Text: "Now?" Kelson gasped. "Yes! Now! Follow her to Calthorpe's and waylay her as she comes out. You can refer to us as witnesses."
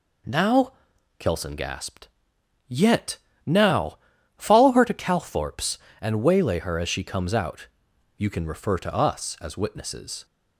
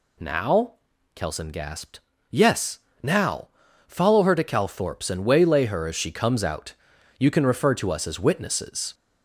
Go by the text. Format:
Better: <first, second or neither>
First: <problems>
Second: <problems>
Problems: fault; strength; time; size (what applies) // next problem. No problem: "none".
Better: second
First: says "Yet" for "Yes"; at 2.6 s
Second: none